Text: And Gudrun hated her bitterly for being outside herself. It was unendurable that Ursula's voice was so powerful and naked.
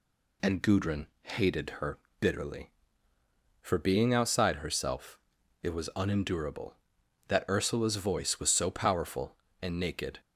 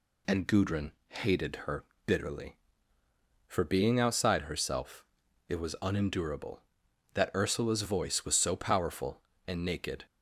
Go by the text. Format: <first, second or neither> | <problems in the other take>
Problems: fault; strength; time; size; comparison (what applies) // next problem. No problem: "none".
neither | pauses between "Gudrun" and "hated"; slight; the same in both // pauses between "her" and "bitterly"; slight; the same in both